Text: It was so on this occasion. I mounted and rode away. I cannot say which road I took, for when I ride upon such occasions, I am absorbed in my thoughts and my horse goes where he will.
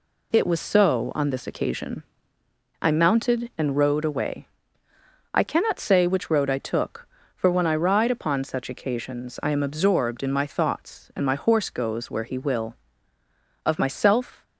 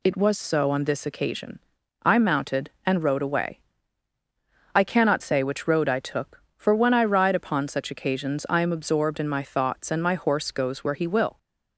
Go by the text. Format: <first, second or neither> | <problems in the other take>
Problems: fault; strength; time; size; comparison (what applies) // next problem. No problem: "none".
second | goes on to say "Of myself"; noticeable; from 13.6 s on; 0.78 s long